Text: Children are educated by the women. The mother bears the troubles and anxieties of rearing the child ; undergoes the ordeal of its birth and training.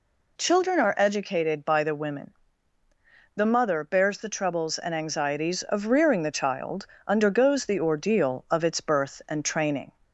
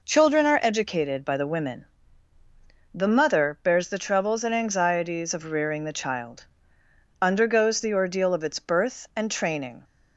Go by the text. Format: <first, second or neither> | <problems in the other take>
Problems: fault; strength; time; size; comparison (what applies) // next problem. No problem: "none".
neither | none